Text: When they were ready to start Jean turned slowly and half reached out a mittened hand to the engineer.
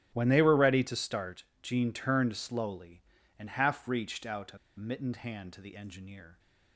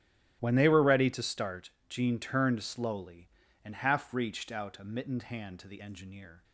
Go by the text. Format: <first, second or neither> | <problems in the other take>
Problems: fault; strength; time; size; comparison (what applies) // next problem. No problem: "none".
second | starts louder than the rest; strong; until 1.1 s; 14.5 dB; strong in the second // pauses between "start" and "Jean"; slight; at 1.4 s; 0.22 s long; slight in the second // pauses between "a" and "mittened"; slight; at 4.5 s; 0.21 s long